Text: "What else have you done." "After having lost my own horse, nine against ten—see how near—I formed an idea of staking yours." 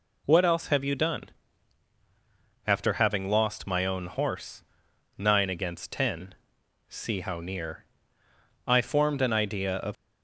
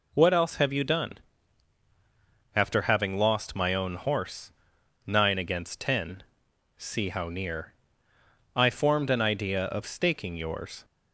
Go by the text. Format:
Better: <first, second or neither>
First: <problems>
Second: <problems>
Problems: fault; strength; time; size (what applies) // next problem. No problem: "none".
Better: second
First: stops before "staking yours"; at 9.9 s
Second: none